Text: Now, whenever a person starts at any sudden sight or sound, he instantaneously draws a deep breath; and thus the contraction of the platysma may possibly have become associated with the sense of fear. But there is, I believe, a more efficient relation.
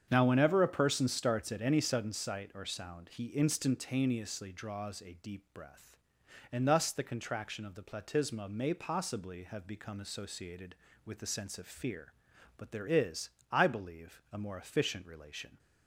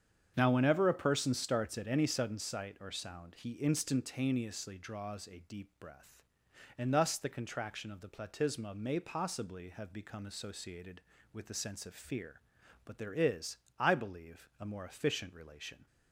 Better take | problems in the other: neither | starts louder than the rest; strong; the same in both

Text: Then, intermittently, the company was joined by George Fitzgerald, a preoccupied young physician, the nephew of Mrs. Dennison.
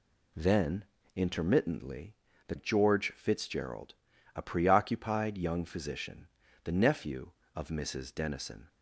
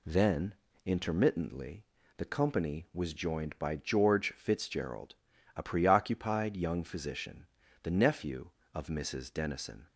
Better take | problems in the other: second | skips "company was joined by"; at 2.5 s

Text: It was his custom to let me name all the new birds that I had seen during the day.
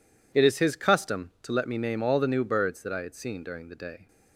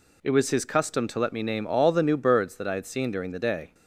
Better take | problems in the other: second | says "is" for "was"; at 0.4 s

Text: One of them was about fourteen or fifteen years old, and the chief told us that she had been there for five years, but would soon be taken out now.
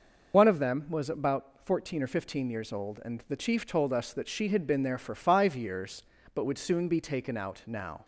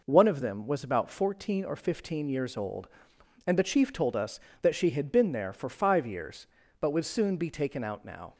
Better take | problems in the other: second | loses the start of "One"; at 0.3 s; 70 ms

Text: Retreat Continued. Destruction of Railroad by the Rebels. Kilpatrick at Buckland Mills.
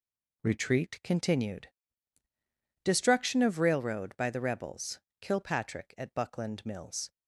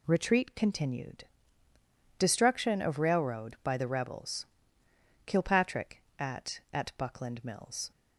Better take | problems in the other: first | says "at" twice; at 6.7 s

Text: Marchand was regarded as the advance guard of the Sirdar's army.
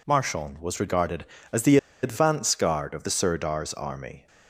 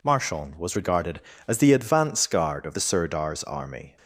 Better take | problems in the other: second | pauses between "the" and "advance"; slight; at 1.7 s; 0.26 s long

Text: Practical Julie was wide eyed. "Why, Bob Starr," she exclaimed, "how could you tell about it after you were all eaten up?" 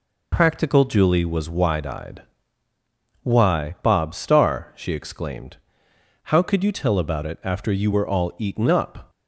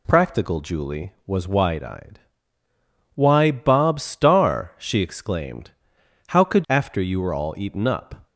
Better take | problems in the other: first | skips "you tell about it"; at 6.6 s

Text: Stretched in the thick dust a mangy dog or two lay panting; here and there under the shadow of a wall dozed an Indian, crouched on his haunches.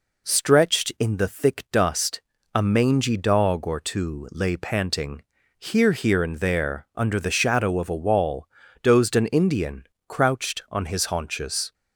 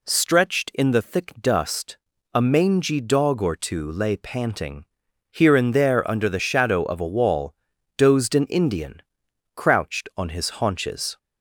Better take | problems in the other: second | pauses between "dust" and "a"; slight; at 2.2 s; 0.32 s long; also in the second // says "here" twice; at 5.9 s // pauses between "wall" and "dozed"; slight; at 8.4 s; 0.36 s long; also in the second

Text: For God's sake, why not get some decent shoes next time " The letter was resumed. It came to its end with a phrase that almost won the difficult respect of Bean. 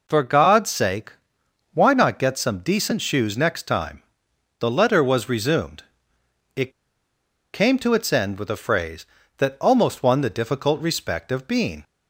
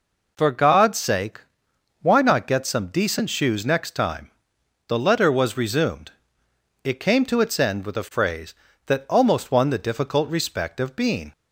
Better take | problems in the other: second | pauses between "It" and "came"; noticeable; at 6.7 s; 0.81 s long

